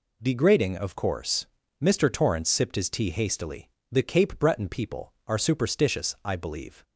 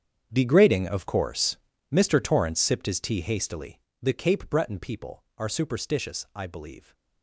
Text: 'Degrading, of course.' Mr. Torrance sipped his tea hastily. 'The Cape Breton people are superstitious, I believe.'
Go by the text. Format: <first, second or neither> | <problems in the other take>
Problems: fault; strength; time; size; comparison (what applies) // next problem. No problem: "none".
first | gets quieter; strong; throughout; 16 dB